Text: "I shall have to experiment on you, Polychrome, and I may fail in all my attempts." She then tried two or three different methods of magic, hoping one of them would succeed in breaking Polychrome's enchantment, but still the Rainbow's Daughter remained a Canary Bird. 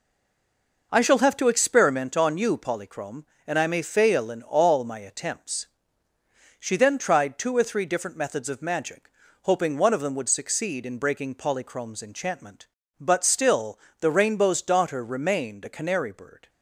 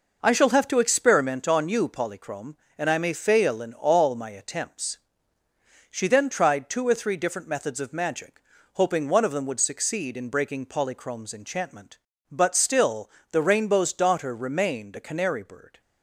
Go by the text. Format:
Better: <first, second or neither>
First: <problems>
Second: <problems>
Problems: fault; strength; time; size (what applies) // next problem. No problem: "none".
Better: second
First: stays silent before the first word; slight; until 0.9 s; 0.9 s long // pauses between "still" and "the"; slight; at 13.7 s; 0.22 s long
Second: pauses between "still" and "the"; slight; at 13.1 s; 0.22 s long